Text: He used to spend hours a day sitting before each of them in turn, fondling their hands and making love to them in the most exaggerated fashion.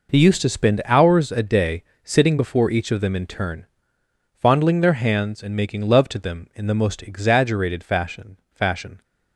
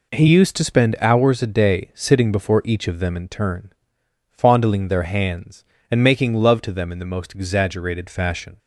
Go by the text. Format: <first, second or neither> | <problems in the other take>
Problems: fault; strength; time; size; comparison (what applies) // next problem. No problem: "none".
second | pauses between "day" and "sitting"; slight; at 1.8 s; 0.18 s long // says "fashion" twice; at 8.5 s